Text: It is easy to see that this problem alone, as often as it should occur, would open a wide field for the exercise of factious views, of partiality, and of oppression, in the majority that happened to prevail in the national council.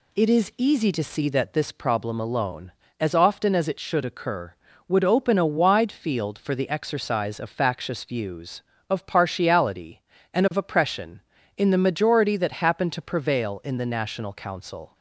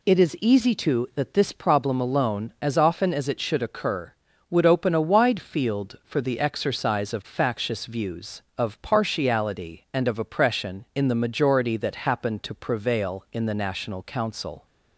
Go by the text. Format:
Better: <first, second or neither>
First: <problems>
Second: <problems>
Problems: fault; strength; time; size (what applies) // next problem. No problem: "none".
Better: first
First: none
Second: skips "see"; at 1.1 s